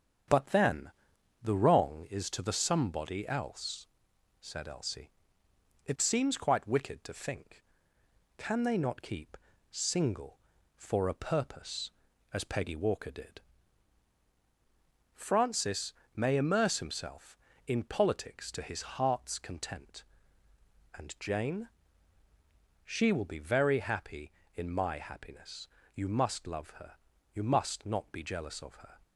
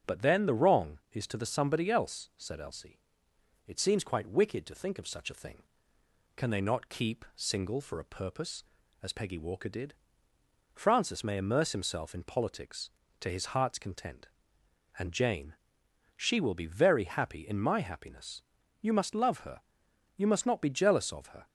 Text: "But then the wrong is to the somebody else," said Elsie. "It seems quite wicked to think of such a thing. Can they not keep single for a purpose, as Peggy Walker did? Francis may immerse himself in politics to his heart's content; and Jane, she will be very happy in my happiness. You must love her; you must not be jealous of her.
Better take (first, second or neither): second